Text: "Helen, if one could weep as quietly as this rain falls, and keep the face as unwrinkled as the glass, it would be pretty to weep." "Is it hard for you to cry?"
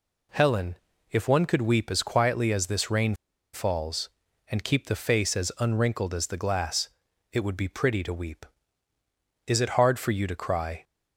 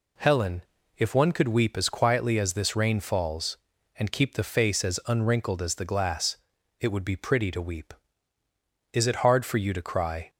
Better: second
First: pauses between "rain" and "falls"; at 3.1 s; 0.37 s long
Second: none

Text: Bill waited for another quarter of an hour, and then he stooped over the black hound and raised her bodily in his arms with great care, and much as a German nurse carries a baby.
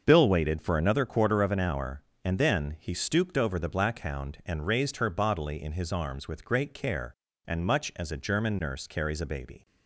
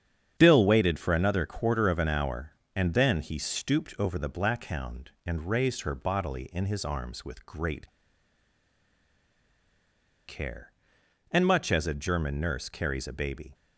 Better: first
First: starts louder than the rest; until 1.0 s; 6.5 dB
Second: starts louder than the rest; strong; until 1.3 s; 8 dB // pauses between "great" and "care"; strong; at 7.8 s; 2.3 s long

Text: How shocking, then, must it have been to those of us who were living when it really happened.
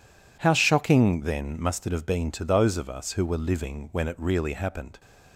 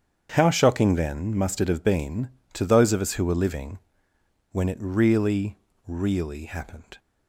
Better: first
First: none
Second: starts louder than the rest; strong; until 1.3 s; 8 dB // pauses between "living" and "when"; noticeable; at 3.7 s; 0.74 s long // says "really" twice; at 5.8 s

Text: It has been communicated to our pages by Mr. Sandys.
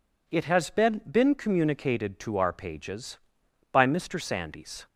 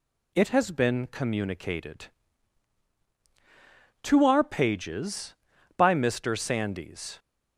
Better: second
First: says "been" twice; at 1.0 s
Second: none

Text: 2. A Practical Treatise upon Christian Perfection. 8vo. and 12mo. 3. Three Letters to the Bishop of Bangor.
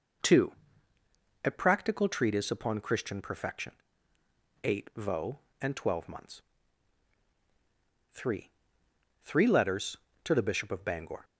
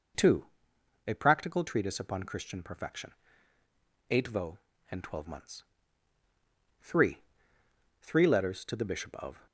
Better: first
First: none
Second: stops before "Bangor"; at 9.4 s

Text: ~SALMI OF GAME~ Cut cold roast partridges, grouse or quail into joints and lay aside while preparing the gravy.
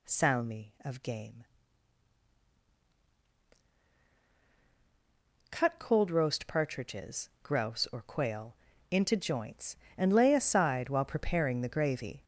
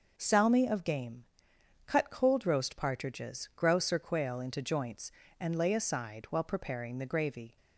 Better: second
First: gets louder; strong; throughout; 7.5 dB // pauses between "quail" and "into"; slight; at 8.5 s; 0.34 s long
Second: none

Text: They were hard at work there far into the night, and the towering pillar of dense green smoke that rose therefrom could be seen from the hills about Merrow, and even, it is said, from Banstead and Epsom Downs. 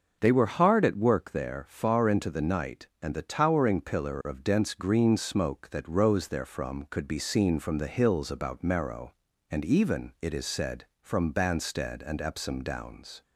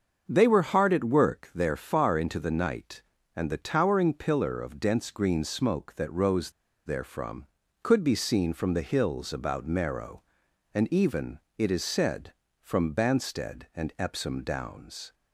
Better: first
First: starts louder than the rest; noticeable; until 1.2 s; 6 dB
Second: starts louder than the rest; until 1.2 s; 6.5 dB // pauses between "rose" and "therefrom"; slight; at 6.5 s; 0.35 s long

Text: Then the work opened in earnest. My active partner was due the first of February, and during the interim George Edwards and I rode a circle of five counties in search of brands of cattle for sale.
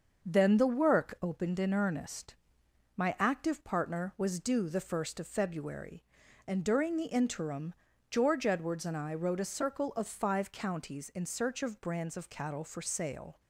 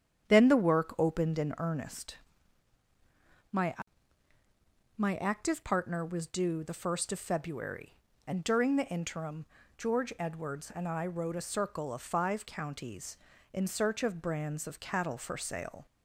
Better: first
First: starts louder than the rest; until 1.2 s; 6.5 dB // pauses between "interim" and "George"; slight; at 7.7 s; 0.34 s long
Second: starts louder than the rest; strong; until 1.3 s; 8.5 dB // says "My" twice; at 4.9 s // pauses between "interim" and "George"; slight; at 9.4 s; 0.32 s long

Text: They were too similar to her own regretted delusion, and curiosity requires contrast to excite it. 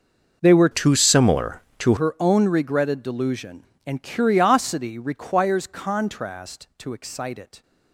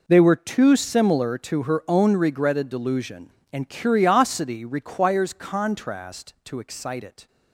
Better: second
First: changes voice from "too" to "to"; from 0.7 to 1.9 s; 1.2 s long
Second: none

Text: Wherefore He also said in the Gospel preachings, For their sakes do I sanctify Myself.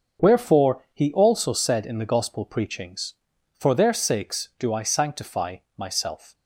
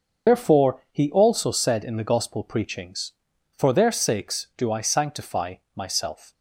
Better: first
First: pauses between "sanctify" and "Myself"; slight; at 5.5 s; 0.20 s long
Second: loses the start of "Wherefore"; at 0.2 s; 90 ms // pauses between "sanctify" and "Myself"; slight; at 5.5 s; 0.20 s long

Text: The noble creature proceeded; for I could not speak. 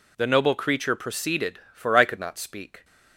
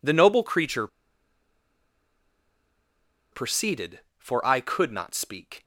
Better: first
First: none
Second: pauses between "creature" and "proceeded"; strong; at 0.8 s; 2.4 s long

